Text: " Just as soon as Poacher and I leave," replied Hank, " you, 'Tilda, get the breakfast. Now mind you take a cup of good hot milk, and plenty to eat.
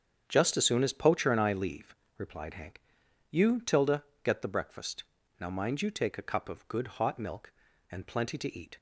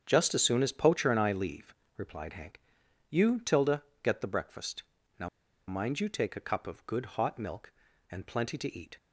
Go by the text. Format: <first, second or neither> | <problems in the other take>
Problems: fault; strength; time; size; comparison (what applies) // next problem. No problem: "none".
first | starts louder than the rest; until 1.0 s; 6 dB; also in the first // pauses between "Now" and "mind"; at 5.2 s; 0.40 s long